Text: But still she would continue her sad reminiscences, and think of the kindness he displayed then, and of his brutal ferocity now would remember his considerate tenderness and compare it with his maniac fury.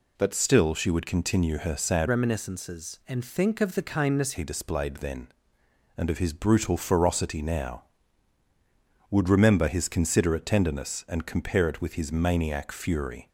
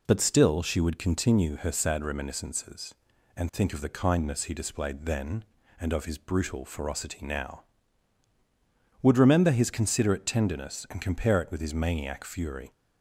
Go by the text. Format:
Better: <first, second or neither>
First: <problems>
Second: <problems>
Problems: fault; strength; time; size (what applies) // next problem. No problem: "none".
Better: second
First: changes voice from "reminiscences" to "kindness"; from 2.0 to 4.3 s; 2.3 s long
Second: none